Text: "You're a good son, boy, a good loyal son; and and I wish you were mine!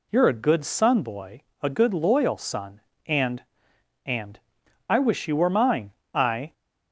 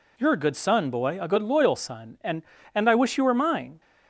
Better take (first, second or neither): second